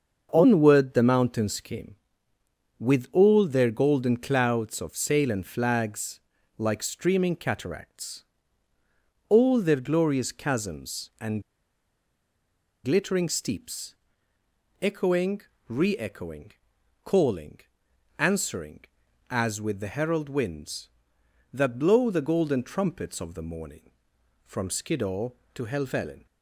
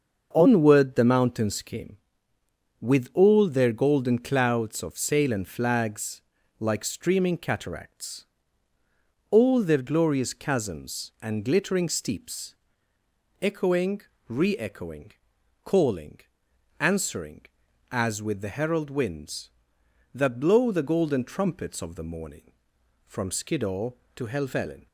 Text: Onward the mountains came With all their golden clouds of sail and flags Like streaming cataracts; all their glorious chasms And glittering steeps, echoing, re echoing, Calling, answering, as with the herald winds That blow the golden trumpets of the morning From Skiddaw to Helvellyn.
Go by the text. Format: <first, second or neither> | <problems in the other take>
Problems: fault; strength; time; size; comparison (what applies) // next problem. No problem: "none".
second | starts louder than the rest; until 1.3 s; 6.5 dB; also in the second // pauses between "flags" and "Like"; slight; at 6.1 s; 0.36 s long; slight in the second // pauses between "And" and "glittering"; strong; at 11.4 s; 1.4 s long